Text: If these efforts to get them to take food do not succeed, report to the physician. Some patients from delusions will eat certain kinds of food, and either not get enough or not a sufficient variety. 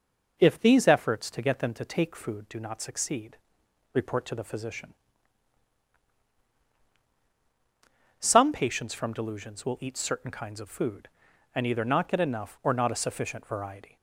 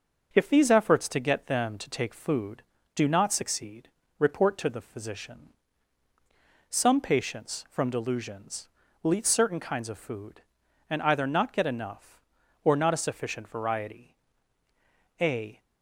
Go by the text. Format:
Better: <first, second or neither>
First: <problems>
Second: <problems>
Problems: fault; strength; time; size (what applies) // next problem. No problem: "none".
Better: first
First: none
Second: starts louder than the rest; until 1.3 s; 6.5 dB // goes on to say "A"; slight; from 15.1 s on; 0.42 s long